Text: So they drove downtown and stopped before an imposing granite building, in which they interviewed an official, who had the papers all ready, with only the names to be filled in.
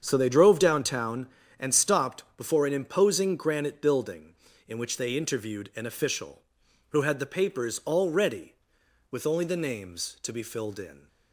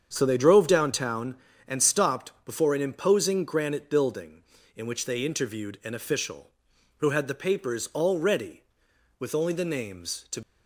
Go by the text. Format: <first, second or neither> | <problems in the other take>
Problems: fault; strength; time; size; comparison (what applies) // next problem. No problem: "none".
first | starts louder than the rest; strong; until 1.1 s; 7.5 dB; strong in the first // stops before "be filled in"; at 10.4 s